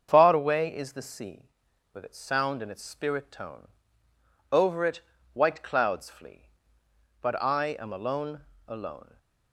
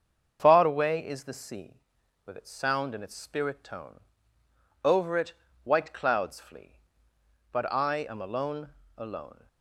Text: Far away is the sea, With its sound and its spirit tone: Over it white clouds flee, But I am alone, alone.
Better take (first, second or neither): neither